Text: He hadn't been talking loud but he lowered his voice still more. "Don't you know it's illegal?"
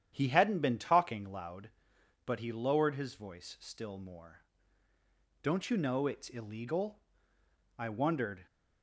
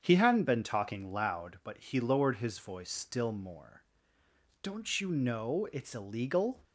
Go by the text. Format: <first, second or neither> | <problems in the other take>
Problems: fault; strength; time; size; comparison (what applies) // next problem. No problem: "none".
second | starts louder than the rest; strong; until 1.1 s; 9.5 dB; strong in the second // goes on to say "I wondered"; noticeable; from 7.7 s on; 0.66 s long